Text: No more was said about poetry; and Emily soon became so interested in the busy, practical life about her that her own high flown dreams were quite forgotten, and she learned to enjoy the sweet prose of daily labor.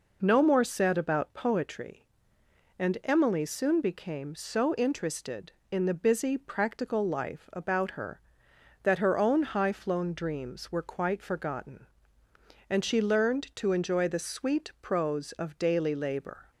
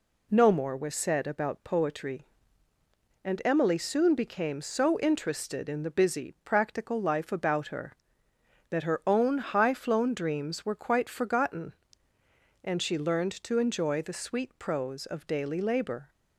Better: second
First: skips "was"; at 0.6 s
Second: none

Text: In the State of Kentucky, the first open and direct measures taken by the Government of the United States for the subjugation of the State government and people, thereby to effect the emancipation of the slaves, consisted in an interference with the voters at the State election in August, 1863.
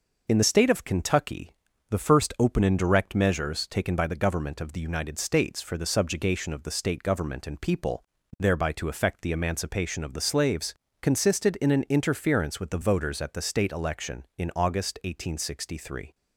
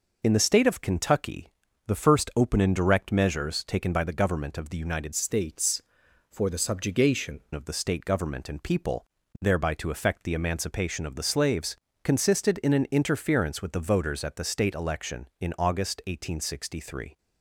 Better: first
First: none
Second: changes voice from "States" to "subjugation"; from 5.1 to 7.3 s; 2.2 s long

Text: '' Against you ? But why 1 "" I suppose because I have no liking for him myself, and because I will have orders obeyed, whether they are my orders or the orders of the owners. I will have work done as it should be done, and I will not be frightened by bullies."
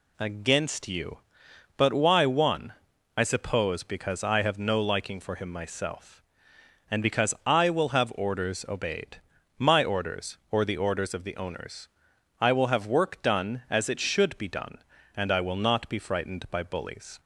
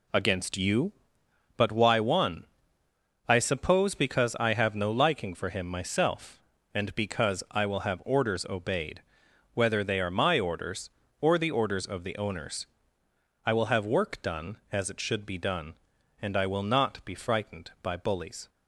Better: second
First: skips "whether they are"; at 9.3 s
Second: none

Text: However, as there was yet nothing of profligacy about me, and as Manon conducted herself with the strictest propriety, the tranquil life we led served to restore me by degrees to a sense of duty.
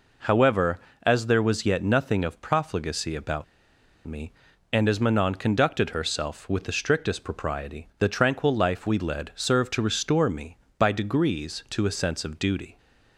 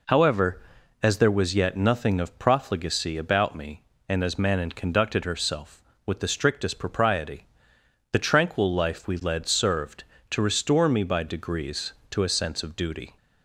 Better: second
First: pauses between "about" and "me"; noticeable; at 3.4 s; 0.62 s long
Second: none

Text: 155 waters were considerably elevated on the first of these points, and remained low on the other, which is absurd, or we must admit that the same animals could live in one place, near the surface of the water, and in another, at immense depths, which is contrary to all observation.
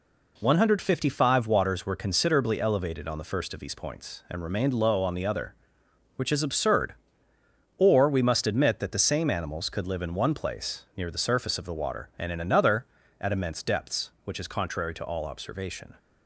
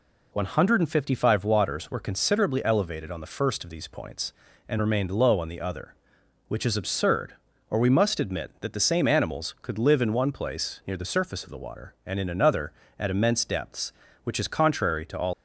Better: first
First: none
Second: stops before "observation"; at 15.3 s

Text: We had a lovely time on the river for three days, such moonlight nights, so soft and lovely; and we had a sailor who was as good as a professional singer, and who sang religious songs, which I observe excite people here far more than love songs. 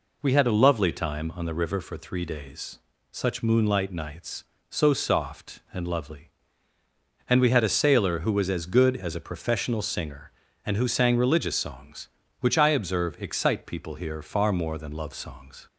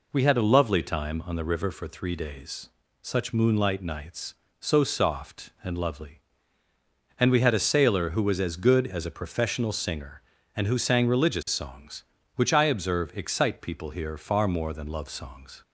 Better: neither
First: none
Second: none

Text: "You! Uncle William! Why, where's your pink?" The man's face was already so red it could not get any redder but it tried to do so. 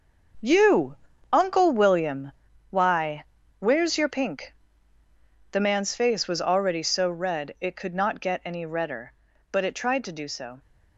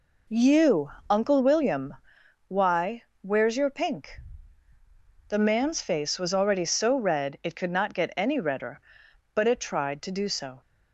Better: second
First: gets quieter; strong; throughout; 10.5 dB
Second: none

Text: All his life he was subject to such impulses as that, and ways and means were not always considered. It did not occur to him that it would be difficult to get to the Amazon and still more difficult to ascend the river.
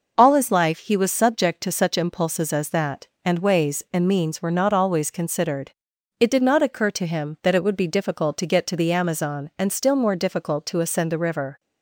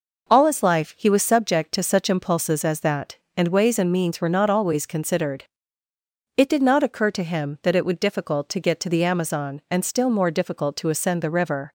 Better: first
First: none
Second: skips "be"; at 7.9 s

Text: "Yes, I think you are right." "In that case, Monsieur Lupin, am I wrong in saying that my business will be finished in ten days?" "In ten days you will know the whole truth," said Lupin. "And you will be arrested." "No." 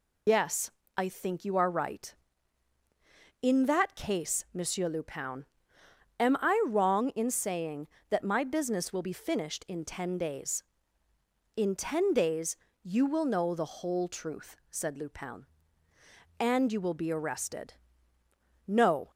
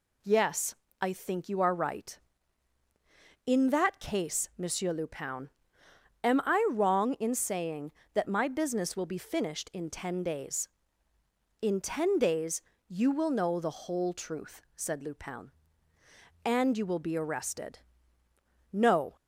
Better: second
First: loses the start of "Yes"; at 0.2 s; 90 ms // pauses between "days" and "you"; slight; at 12.5 s; 0.30 s long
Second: pauses between "days" and "you"; slight; at 12.5 s; 0.30 s long

